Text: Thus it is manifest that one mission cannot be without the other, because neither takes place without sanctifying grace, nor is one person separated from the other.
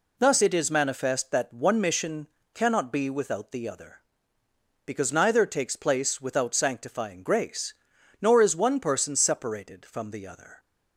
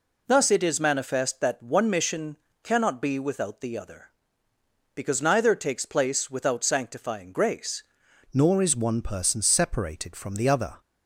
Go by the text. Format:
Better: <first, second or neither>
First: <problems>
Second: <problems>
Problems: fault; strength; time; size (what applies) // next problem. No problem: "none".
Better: first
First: pauses between "mission" and "cannot"; slight; at 2.2 s; 0.26 s long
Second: pauses between "mission" and "cannot"; slight; at 2.3 s; 0.26 s long // changes voice at "nor"; from 8.3 s on; 2.4 s long